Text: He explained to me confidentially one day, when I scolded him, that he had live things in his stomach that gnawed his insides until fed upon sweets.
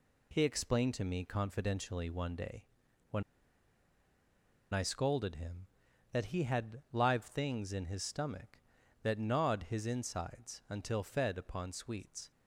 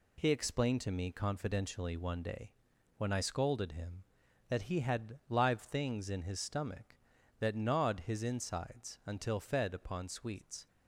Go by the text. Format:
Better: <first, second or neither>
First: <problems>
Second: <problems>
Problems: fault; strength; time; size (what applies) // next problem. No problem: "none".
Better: second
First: pauses between "when" and "I"; strong; at 3.2 s; 1.5 s long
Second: none